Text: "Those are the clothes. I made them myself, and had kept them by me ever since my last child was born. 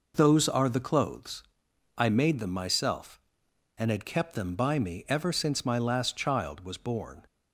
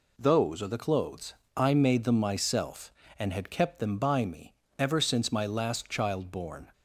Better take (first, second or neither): first